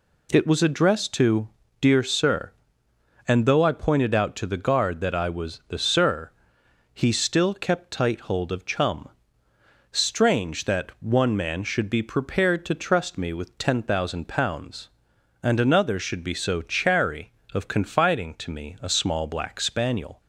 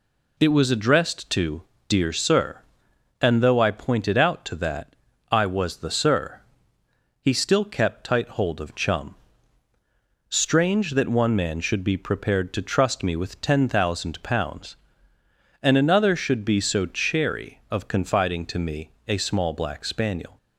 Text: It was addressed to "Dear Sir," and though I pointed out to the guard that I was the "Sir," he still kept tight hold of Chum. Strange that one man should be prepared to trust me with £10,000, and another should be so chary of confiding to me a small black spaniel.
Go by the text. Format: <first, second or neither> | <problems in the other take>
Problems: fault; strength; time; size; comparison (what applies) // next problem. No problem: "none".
first | pauses between "to" and "Dear"; slight; at 1.6 s; 0.26 s long; slight in the first // skips "the guard"; at 4.5 s // pauses between "that" and "I"; slight; at 4.9 s; 0.36 s long // pauses between "me" and "a"; slight; at 18.9 s; 0.16 s long